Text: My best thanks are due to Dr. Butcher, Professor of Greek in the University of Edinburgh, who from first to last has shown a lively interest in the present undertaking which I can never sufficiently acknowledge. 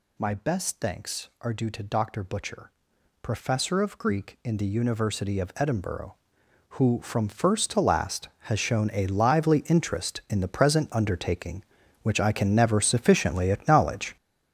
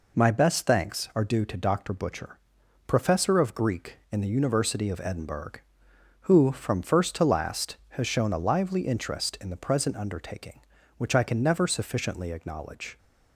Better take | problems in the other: second | gets louder; strong; throughout; 9.5 dB

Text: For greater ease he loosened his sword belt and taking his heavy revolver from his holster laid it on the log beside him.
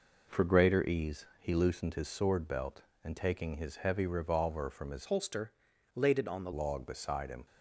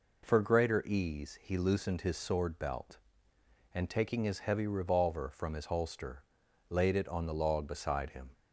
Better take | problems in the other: second | changes voice from "holster" to "the"; from 5.0 to 6.5 s; 1.5 s long // pauses between "holster" and "laid"; at 5.5 s; 0.42 s long; noticeable in the second

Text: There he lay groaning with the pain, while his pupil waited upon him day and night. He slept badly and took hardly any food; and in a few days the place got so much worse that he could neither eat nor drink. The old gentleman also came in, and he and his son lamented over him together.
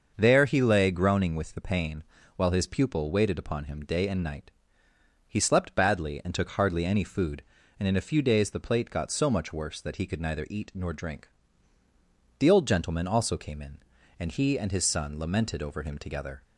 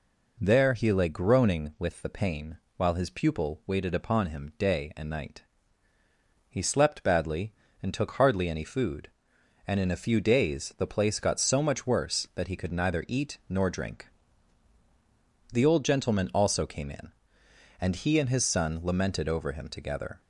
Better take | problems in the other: second | starts louder than the rest; until 1.1 s; 6.5 dB // says "plate" for "place"; at 8.5 s

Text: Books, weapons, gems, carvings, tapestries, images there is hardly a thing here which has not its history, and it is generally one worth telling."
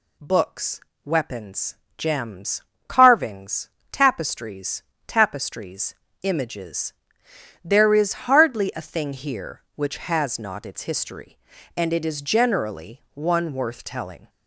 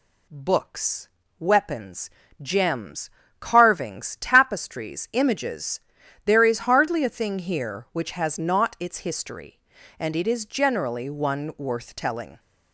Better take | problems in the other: second | says "tapestries" twice; at 5.0 s // pauses between "images" and "there"; noticeable; at 6.9 s; 0.72 s long; noticeable in the second

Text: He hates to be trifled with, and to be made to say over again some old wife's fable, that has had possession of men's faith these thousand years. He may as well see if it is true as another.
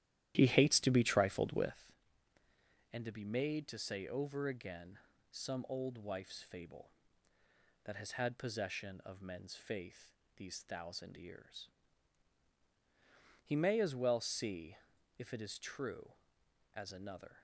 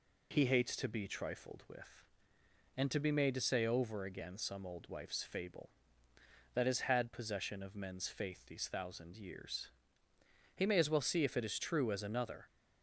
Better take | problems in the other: second | starts louder than the rest; strong; until 1.8 s; 12.5 dB // pauses between "again" and "some"; slight; at 4.9 s; 0.32 s long // pauses between "faith" and "these"; slight; at 10.1 s; 0.24 s long // pauses between "see" and "if"; at 14.7 s; 0.42 s long

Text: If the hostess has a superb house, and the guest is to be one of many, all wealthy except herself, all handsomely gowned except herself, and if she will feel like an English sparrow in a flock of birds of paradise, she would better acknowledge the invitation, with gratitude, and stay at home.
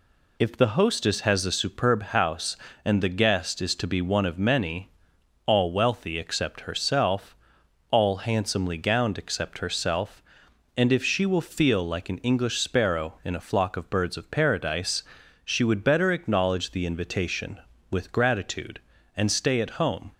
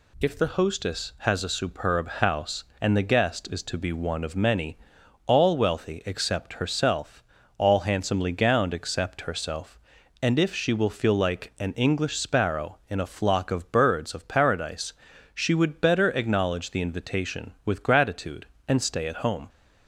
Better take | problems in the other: neither | none

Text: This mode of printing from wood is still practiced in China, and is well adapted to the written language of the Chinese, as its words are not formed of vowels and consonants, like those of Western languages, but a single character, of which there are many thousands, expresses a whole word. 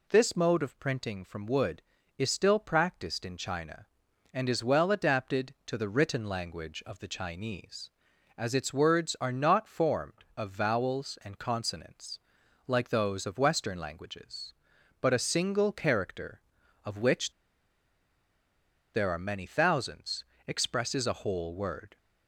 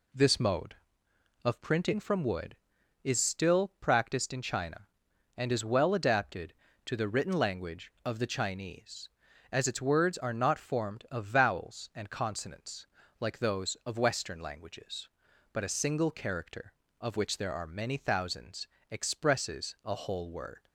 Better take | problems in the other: second | pauses between "which" and "there"; strong; at 17.3 s; 1.6 s long

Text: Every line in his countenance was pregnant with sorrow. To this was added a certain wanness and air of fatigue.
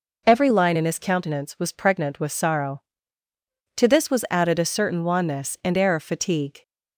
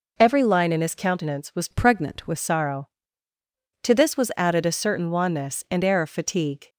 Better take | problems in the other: first | changes voice from "pregnant" to "with"; from 1.7 to 2.3 s; 0.6 s long

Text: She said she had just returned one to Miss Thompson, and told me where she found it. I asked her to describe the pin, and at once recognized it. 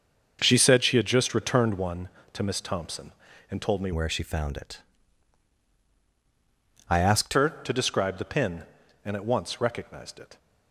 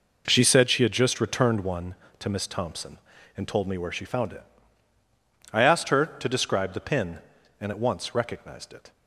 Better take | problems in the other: second | starts louder than the rest; until 1.4 s; 6.5 dB // changes voice from "where" to "asked"; from 3.9 to 7.3 s; 3.4 s long

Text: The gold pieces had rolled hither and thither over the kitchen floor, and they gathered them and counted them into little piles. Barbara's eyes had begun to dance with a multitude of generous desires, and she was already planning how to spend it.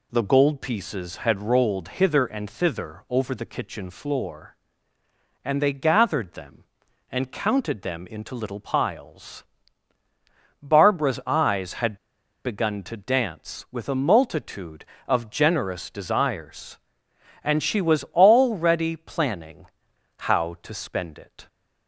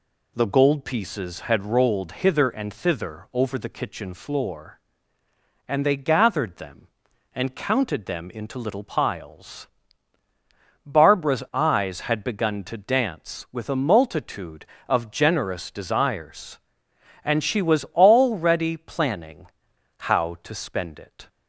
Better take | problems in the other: second | pauses between "had" and "begun"; noticeable; at 11.9 s; 0.49 s long // pauses between "planning" and "how"; noticeable; at 19.6 s; 0.50 s long; noticeable in the second

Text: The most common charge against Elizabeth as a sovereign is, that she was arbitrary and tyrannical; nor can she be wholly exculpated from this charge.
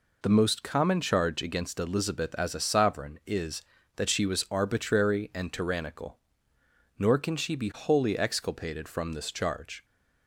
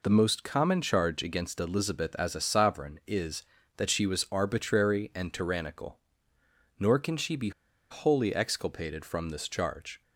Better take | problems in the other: first | pauses between "be" and "wholly"; at 7.4 s; 0.40 s long

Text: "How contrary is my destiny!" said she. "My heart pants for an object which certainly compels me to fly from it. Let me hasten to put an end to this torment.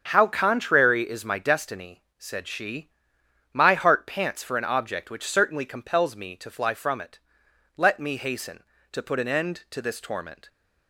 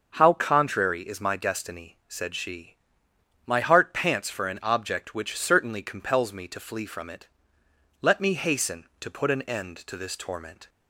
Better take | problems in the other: first | starts louder than the rest; until 1.1 s; 6.5 dB; also in the first // says "flee" for "fly"; at 6.6 s

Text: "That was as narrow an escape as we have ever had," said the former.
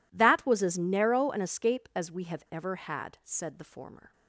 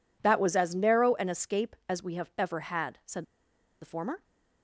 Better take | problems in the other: first | pauses between "said" and "the"; noticeable; at 3.2 s; 0.56 s long

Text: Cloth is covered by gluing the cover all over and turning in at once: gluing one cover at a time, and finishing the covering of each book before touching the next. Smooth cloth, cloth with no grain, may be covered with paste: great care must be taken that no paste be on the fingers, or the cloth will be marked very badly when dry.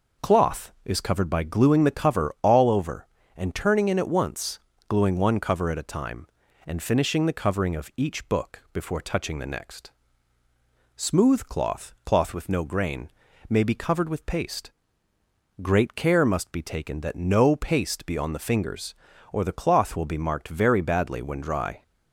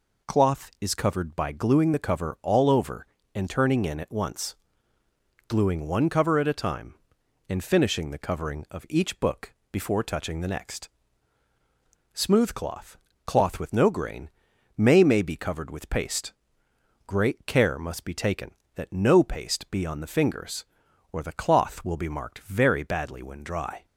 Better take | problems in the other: first | pauses between "book" and "before"; slight; at 9.5 s; 0.16 s long // says "may" twice; at 15.0 s

